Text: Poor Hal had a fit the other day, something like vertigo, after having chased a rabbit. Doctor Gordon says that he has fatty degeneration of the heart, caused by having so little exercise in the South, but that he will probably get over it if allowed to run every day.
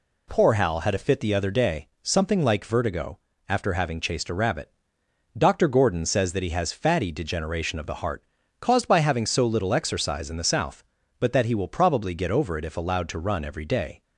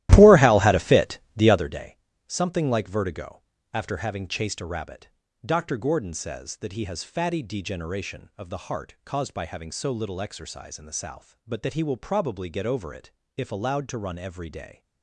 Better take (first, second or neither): first